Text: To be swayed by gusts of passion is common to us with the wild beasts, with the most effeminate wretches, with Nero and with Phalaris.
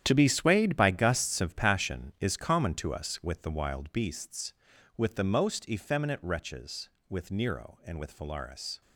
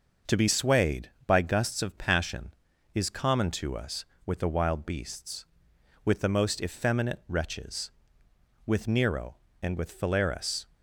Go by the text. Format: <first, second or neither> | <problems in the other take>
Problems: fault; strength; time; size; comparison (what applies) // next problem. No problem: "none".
second | gets quieter; strong; throughout; 12.5 dB // starts louder than the rest; strong; until 1.0 s; 10 dB; noticeable in the second